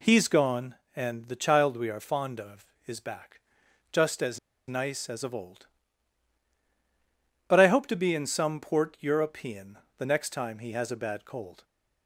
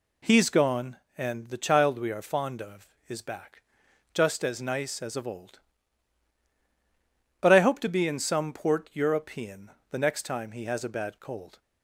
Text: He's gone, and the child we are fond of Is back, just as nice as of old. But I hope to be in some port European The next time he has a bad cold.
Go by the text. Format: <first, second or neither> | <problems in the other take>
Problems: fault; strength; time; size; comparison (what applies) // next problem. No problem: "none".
second | pauses between "as" and "nice"; slight; at 4.3 s; 0.29 s long // pauses between "European" and "The"; slight; at 9.7 s; 0.18 s long; slight in the second